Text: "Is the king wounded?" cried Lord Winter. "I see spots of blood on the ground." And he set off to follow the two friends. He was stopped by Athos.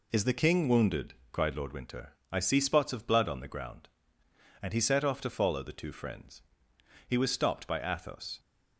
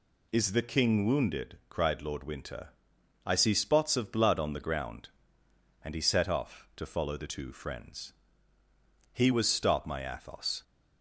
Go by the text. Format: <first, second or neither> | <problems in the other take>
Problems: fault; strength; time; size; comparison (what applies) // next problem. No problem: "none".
first | says "my" for "by"; at 9.8 s